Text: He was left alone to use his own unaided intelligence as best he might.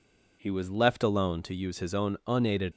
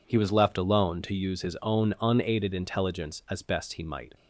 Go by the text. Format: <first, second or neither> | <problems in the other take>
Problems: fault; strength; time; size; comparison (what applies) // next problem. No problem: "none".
second | stops before "intelligence as best he might"; at 2.7 s